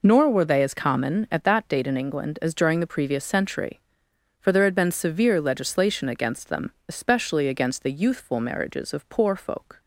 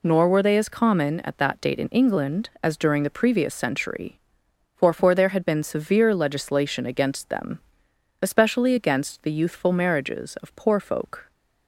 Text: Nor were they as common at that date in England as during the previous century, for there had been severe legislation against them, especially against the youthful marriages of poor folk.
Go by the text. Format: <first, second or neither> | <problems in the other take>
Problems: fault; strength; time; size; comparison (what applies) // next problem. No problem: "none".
first | says "for" twice; at 4.9 s